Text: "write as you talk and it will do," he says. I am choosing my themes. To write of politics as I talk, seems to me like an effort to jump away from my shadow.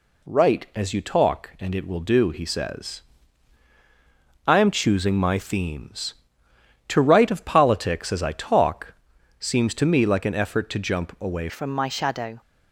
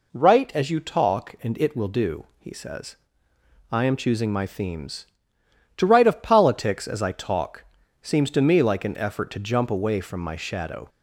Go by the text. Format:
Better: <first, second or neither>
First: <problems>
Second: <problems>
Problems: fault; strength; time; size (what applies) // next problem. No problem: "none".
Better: second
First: changes voice at "from"; from 11.4 s on; 1.0 s long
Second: none